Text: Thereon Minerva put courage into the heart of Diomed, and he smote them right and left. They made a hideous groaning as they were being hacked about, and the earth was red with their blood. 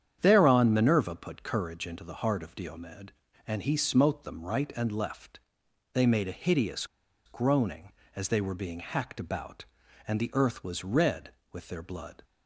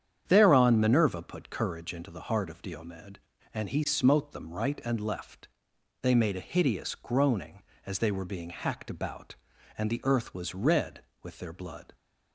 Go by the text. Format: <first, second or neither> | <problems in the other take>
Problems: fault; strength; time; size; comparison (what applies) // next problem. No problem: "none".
second | starts louder than the rest; strong; until 1.2 s; 9 dB; strong in the second // pauses between "hideous" and "groaning"; at 6.8 s; 0.40 s long